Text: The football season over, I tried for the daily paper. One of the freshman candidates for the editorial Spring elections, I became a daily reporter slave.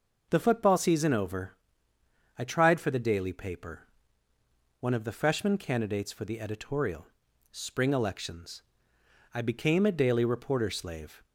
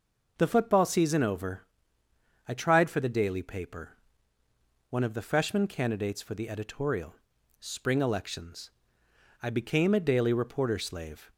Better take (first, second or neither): neither